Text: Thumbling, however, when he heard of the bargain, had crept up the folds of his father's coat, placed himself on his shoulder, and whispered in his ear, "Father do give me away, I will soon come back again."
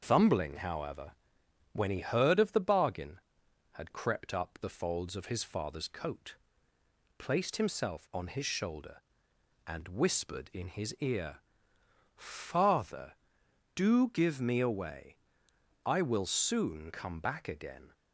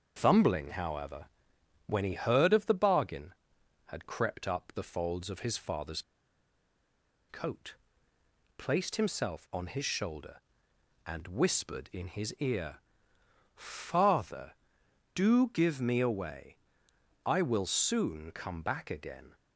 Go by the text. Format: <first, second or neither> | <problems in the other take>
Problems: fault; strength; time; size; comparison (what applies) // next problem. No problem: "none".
first | starts louder than the rest; until 1.2 s; 6.5 dB; also in the first // pauses between "father's" and "coat"; strong; at 6.0 s; 1.2 s long